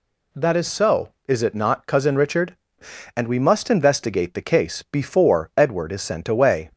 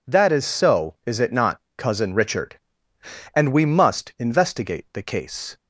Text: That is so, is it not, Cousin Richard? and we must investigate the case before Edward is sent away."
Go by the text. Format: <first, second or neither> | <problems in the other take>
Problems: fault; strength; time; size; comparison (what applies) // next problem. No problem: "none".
first | stops before "before Edward is sent away"; at 5.5 s